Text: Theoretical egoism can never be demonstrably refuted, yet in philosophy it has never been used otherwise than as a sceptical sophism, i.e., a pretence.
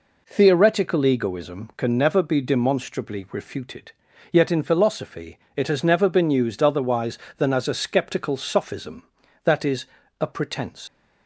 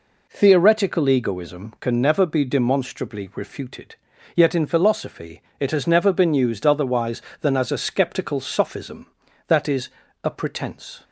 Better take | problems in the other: second | pauses between "philosophy" and "it"; slight; at 5.3 s; 0.16 s long; slight in the second // leaves "pretence" unfinished; at 10.8 s; 125 ms

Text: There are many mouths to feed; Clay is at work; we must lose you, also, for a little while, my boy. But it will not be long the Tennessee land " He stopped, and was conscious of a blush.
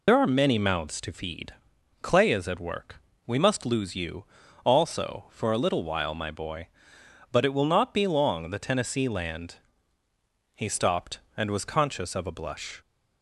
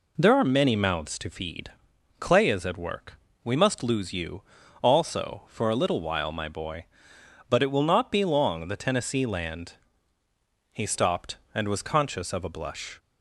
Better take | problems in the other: second | loses the start of "There"; at 0.0 s; 80 ms

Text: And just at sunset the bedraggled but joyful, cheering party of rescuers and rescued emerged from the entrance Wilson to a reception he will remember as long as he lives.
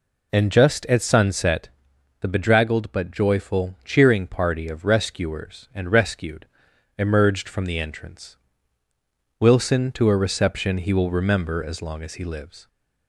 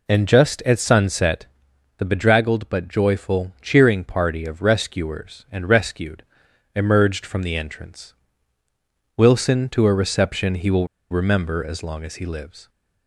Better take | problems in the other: first | pauses between "sunset" and "the"; noticeable; at 1.4 s; 0.52 s long; noticeable in the first // pauses between "rescued" and "emerged"; noticeable; at 6.2 s; 0.54 s long; noticeable in the first // pauses between "entrance" and "Wilson"; at 8.1 s; 1.0 s long; also in the first // pauses between "will" and "remember"; slight; at 10.8 s; 0.24 s long

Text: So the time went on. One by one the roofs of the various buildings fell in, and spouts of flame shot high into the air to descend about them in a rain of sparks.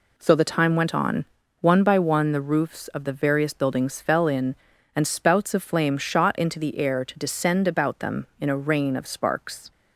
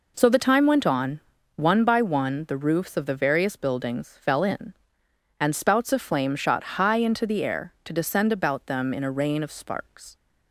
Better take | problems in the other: second | skips "high"; at 6.3 s

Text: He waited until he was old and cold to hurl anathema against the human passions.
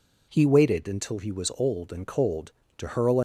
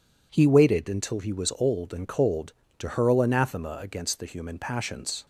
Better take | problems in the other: second | stops before "anathema against the human passions"; at 3.1 s

